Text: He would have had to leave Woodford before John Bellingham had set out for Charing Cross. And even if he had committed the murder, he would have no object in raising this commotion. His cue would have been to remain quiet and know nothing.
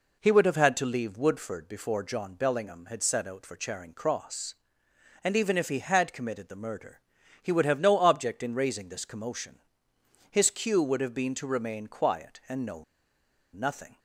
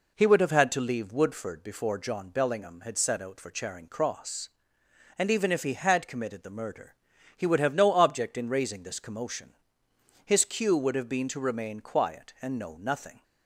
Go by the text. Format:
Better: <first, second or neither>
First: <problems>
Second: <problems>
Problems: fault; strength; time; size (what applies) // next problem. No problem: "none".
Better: second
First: pauses between "know" and "nothing"; noticeable; at 12.8 s; 0.70 s long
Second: none